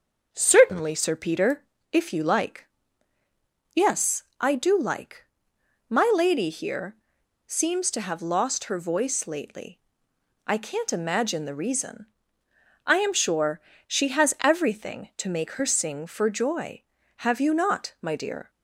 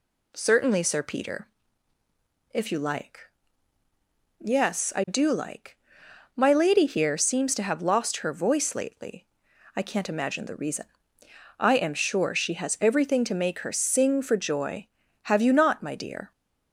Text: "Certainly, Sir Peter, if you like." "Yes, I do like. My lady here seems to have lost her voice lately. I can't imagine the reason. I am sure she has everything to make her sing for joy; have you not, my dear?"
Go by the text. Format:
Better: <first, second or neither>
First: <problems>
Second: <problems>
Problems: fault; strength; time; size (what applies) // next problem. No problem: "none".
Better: second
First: starts louder than the rest; until 1.3 s; 6.5 dB // pauses between "here" and "seems"; noticeable; at 6.9 s; 0.50 s long // pauses between "sure" and "she"; slight; at 13.5 s; 0.26 s long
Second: none